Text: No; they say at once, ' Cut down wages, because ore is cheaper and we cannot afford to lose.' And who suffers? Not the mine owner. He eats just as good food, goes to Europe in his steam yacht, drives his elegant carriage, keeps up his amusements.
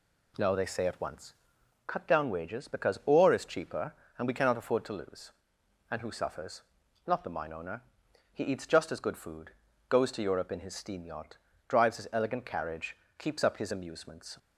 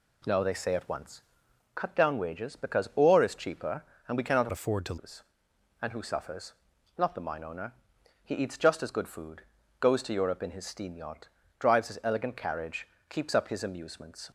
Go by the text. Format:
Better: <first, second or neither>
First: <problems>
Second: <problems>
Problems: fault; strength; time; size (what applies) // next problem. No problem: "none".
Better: first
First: none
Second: changes voice from "afford" to "to"; from 4.5 to 4.9 s; 0.4 s long